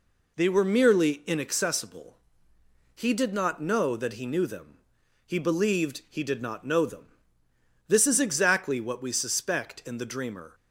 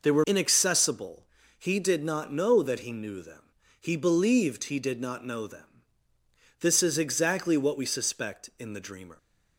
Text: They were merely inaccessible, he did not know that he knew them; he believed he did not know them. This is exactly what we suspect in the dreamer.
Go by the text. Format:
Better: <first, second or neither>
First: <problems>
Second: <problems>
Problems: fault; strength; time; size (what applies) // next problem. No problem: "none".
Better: first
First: none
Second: skips "merely"; at 0.2 s